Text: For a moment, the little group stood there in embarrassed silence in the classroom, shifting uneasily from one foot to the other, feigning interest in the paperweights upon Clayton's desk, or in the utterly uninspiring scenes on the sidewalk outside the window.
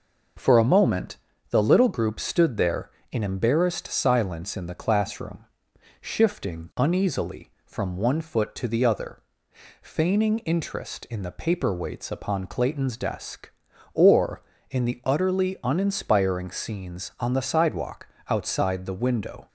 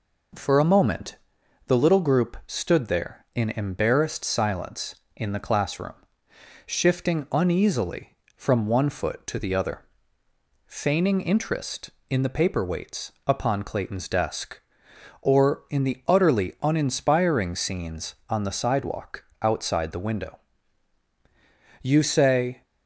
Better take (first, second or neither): first